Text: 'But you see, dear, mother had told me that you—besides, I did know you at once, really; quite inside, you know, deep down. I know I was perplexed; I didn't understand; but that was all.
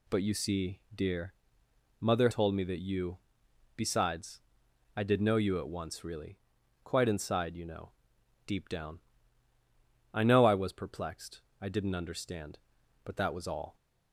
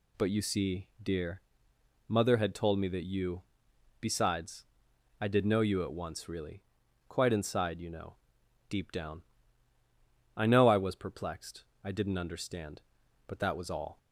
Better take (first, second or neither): second